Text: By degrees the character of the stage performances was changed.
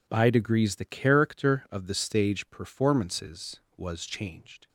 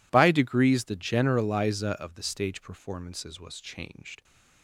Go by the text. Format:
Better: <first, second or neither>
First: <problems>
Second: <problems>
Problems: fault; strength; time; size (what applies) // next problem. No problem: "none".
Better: first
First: none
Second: says "generaliza" for "character"; at 0.9 s